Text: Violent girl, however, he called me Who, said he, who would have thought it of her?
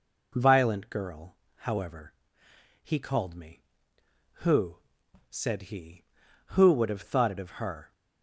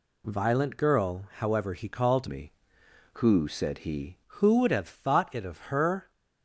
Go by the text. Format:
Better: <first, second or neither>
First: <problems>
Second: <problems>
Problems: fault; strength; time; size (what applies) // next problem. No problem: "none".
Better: first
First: none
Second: changes voice from "me" to "he"; from 2.2 to 4.1 s; 1.9 s long